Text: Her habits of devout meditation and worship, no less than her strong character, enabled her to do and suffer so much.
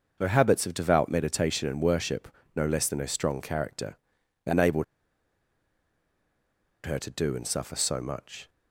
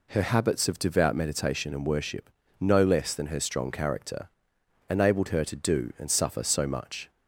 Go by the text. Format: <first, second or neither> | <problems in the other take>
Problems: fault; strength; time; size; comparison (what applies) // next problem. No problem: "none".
second | starts louder than the rest; noticeable; until 1.2 s; 6 dB // pauses between "enabled" and "her"; strong; at 4.8 s; 2.0 s long